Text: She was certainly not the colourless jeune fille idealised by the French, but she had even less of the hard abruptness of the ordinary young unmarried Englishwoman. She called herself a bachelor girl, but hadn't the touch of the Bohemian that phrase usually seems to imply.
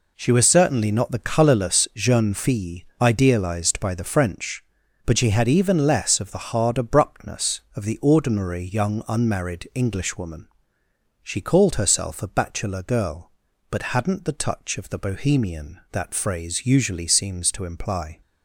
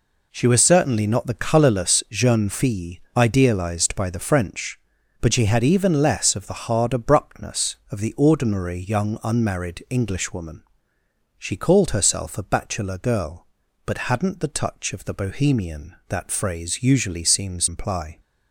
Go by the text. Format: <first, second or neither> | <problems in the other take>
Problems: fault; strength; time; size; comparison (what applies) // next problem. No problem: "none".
first | pauses between "fille" and "idealised"; slight; at 2.9 s; 0.20 s long; slight in the first // skips "to"; at 17.6 s